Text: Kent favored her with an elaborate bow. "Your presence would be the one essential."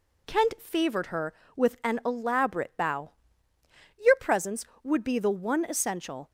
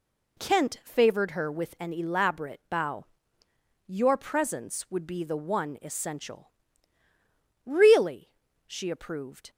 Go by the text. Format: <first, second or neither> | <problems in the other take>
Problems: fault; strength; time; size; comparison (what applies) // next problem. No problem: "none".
first | goes on to say "Really she approved"; strong; from 7.6 s on; 1.8 s long